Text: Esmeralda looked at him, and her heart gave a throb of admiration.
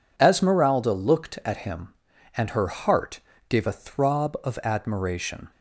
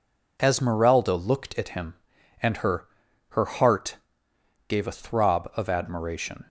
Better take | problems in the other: first | says "her" twice; at 3.2 s // pauses between "heart" and "gave"; noticeable; at 3.9 s; 0.72 s long; slight in the first

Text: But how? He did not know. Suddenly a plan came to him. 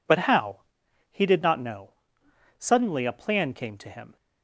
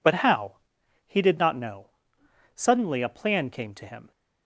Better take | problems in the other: neither | none

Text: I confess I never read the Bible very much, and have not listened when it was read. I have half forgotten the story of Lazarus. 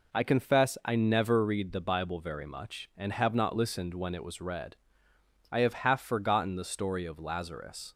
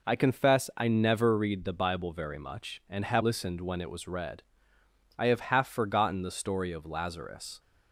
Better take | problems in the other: first | skips "not"; at 3.2 s

